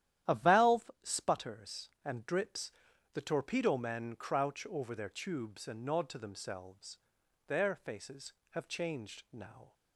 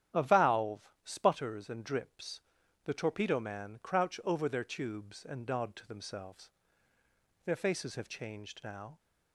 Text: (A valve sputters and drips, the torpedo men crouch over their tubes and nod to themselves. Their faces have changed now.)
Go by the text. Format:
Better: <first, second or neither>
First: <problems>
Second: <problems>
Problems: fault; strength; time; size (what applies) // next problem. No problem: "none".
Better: first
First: starts louder than the rest; strong; until 1.4 s; 11.5 dB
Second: starts louder than the rest; strong; until 1.3 s; 10.5 dB // pauses between "valve" and "sputters"; slight; at 0.8 s; 0.16 s long // says "man" for "men"; at 3.3 s